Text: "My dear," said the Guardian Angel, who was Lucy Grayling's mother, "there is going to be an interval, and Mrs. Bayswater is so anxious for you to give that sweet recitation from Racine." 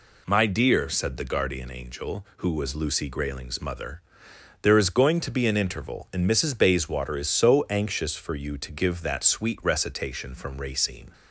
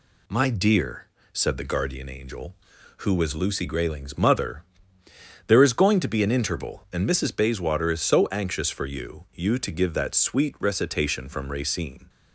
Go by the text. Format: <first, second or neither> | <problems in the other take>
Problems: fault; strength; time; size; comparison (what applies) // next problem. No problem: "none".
first | says "you" twice; at 9.3 s